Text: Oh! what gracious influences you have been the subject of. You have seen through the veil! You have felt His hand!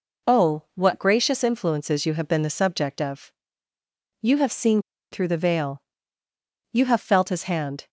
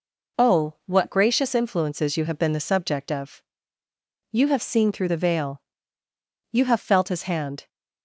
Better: second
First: pauses between "seen" and "through"; slight; at 4.8 s; 0.30 s long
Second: none

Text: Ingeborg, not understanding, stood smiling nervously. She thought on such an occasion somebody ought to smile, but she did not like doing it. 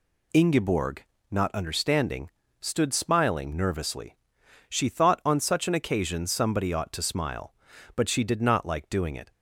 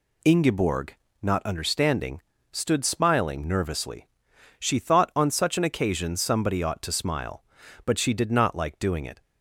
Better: neither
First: none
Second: none

